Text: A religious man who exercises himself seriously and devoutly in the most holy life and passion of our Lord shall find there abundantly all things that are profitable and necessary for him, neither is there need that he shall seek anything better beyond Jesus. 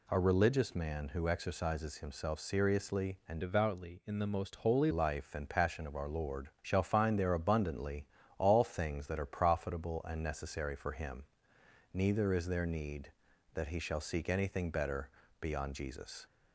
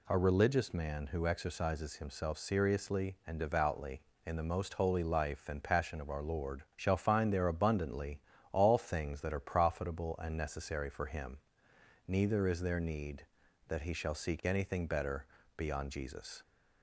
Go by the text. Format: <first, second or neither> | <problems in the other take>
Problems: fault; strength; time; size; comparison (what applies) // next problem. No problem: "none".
second | changes voice from "devoutly" to "holy"; from 3.4 to 4.9 s; 1.5 s long // pauses between "Lord" and "shall"; slight; at 6.4 s; 0.16 s long; slight in the second // pauses between "abundantly" and "all"; slight; at 8.0 s; 0.32 s long; slight in the second // pauses between "better" and "beyond"; slight; at 15.0 s; 0.32 s long; slight in the second